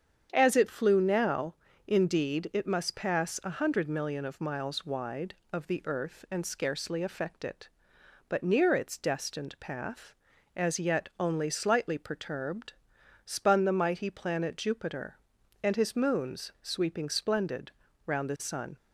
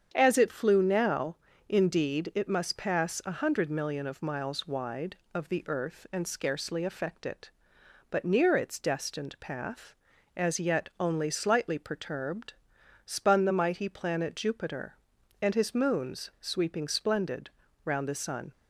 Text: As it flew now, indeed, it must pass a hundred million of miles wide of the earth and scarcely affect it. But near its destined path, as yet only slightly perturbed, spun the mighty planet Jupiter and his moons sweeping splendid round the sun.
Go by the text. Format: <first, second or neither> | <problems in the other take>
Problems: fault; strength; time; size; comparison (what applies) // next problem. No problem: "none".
neither | starts louder than the rest; strong; the same in both // pauses between "splendid" and "round"; slight; the same in both